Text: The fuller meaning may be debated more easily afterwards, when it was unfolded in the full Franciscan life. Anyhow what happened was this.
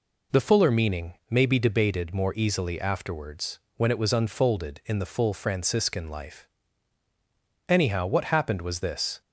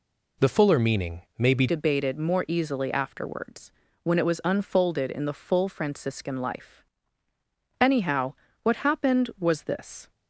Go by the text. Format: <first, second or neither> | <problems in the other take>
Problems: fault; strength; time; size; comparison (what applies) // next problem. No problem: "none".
first | changes voice at "debated"; from 1.6 s on; 8.5 s long // pauses between "Anyhow" and "what"; slight; at 8.3 s; 0.30 s long